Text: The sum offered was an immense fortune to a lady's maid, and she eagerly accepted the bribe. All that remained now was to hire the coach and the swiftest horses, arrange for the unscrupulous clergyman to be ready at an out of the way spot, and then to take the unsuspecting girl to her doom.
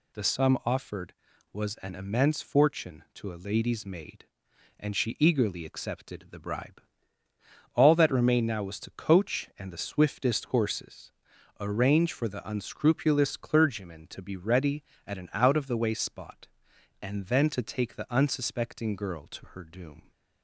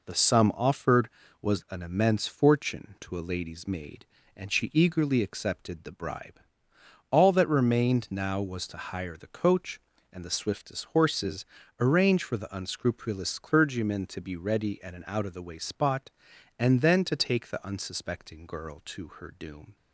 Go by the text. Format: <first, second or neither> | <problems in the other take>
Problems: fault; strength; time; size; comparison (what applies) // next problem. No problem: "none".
second | skips "hire the"; at 8.9 s